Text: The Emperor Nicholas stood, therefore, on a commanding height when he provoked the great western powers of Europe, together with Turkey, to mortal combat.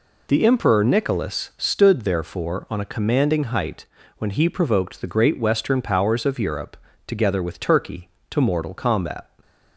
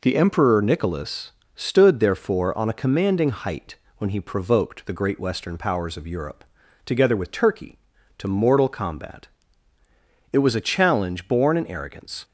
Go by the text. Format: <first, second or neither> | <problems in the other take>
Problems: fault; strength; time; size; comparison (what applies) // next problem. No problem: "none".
first | pauses between "Nicholas" and "stood"; slight; at 1.3 s; 0.22 s long // pauses between "height" and "when"; slight; at 3.7 s; 0.24 s long; slight in the first // goes on to say "It was a challenge born in arrogance"; strong; from 10.3 s on; 1.9 s long